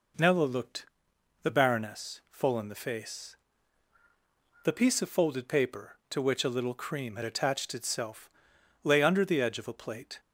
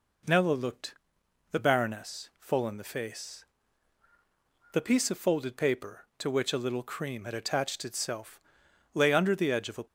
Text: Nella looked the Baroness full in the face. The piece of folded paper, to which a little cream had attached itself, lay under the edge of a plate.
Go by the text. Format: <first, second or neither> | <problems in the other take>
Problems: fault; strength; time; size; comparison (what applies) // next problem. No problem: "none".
first | pauses between "looked" and "the"; noticeable; at 0.9 s; 0.58 s long; noticeable in the first // stops before "plate"; at 9.8 s